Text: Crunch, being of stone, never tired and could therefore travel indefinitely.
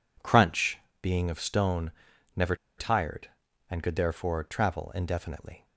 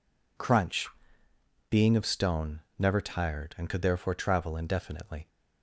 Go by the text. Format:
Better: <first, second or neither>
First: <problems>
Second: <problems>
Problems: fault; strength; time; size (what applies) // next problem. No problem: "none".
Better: second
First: pauses between "never" and "tired"; slight; at 2.5 s; 0.21 s long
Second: none